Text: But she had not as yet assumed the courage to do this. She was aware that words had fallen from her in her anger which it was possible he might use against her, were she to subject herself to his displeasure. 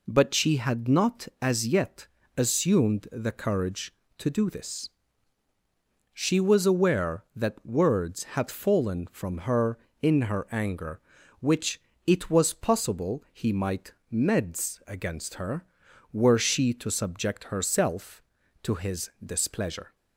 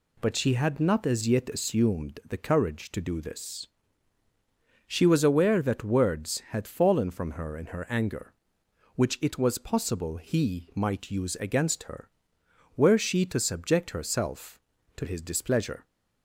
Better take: second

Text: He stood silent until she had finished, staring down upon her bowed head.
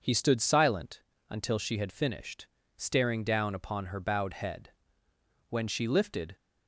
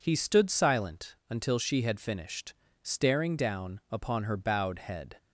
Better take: second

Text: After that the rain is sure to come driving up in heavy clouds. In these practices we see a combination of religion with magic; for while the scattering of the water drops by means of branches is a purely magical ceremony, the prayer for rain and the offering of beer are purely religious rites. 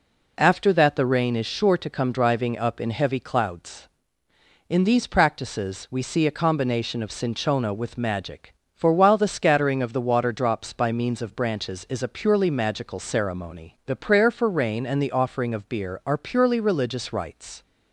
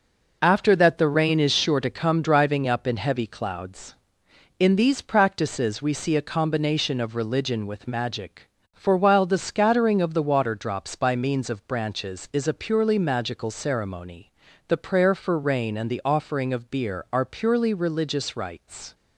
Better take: second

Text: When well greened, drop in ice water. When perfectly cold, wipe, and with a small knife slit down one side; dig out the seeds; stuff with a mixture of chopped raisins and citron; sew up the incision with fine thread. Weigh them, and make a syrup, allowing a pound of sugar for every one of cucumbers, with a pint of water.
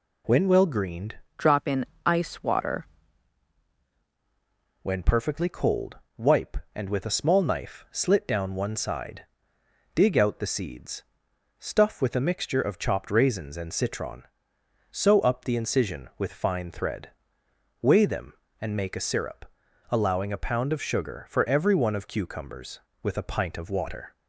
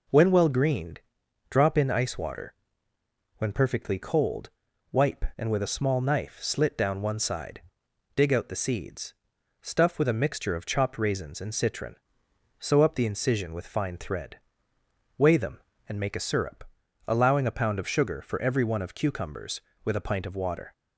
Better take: second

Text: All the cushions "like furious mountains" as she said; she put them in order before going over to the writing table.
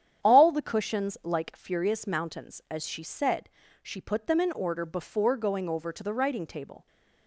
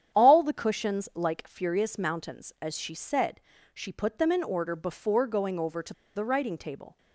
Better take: first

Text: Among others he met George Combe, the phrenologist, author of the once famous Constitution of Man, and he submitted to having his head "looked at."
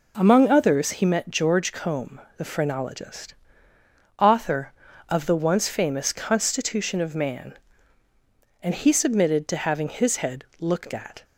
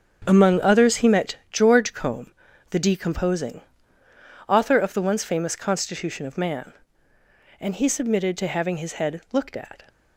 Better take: first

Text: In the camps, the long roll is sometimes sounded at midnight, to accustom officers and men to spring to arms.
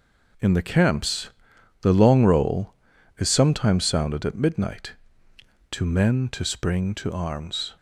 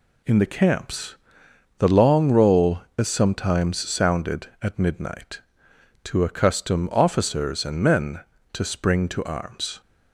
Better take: second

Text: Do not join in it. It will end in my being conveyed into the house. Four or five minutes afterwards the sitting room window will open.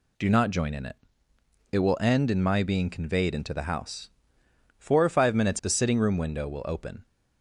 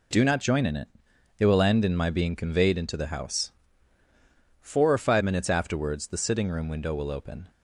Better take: second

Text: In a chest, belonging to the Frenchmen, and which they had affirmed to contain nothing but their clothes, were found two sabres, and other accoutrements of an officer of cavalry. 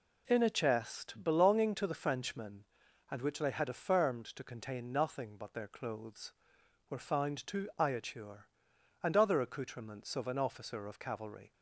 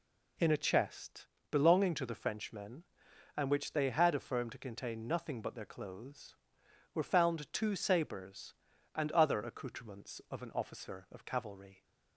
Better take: second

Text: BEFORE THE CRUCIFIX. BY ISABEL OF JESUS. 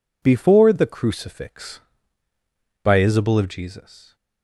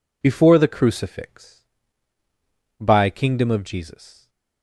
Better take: first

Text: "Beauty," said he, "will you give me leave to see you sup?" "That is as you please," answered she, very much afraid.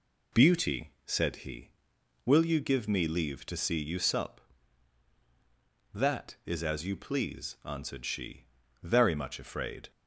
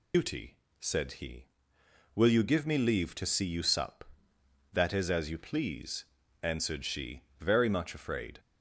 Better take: first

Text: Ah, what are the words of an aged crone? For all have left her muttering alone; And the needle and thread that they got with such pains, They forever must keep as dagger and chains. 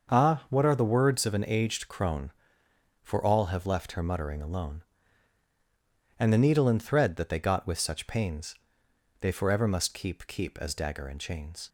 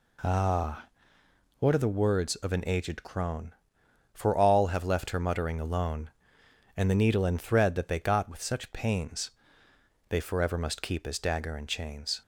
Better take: second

